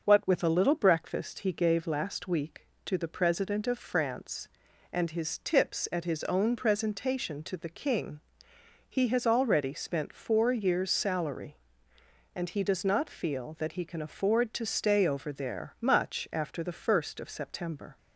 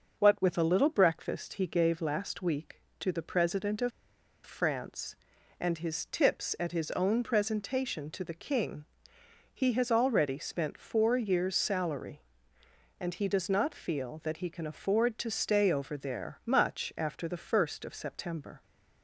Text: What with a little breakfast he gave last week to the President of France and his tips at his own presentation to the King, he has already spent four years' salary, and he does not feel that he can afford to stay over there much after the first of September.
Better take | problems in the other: first | pauses between "of" and "France"; noticeable; at 3.9 s; 0.55 s long

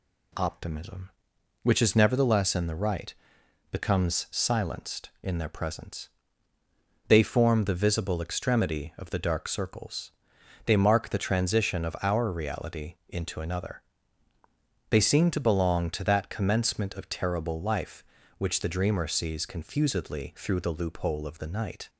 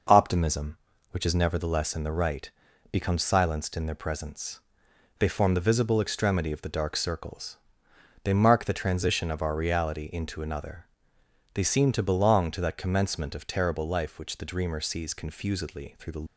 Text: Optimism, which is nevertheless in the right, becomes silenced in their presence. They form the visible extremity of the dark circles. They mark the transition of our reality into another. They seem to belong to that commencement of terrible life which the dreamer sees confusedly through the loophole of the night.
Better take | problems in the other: first | stops before "loophole of the night"; at 16.2 s

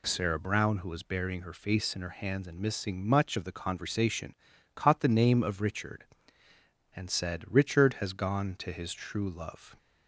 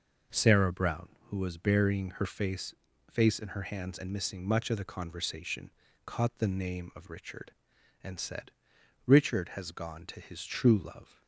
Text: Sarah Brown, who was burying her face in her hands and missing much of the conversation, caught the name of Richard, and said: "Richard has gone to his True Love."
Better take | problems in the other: first | says "face" twice; at 3.0 s

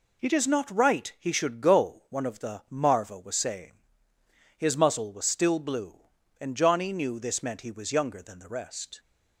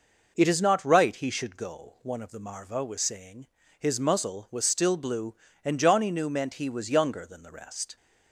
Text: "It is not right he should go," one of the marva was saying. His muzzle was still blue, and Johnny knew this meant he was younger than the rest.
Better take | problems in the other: first | skips "this"; at 6.2 s

